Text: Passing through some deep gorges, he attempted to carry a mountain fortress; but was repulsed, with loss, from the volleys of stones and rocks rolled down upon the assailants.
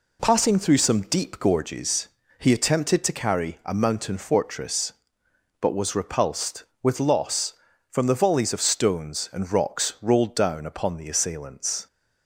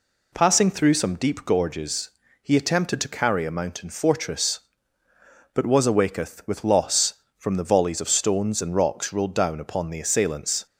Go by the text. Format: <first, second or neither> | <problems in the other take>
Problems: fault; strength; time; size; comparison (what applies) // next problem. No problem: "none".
first | says "awaketh" for "repulsed"; at 5.8 s